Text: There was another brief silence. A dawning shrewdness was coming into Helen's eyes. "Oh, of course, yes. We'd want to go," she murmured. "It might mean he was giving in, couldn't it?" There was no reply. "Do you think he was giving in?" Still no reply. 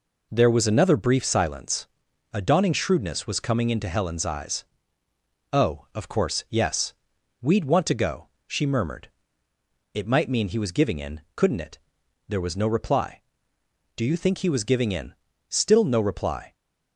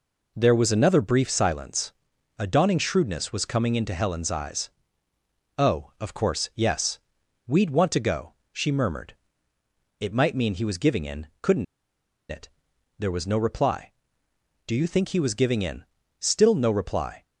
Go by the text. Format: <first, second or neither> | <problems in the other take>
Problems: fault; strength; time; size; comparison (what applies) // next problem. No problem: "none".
first | pauses between "couldn't" and "it"; noticeable; at 11.6 s; 0.66 s long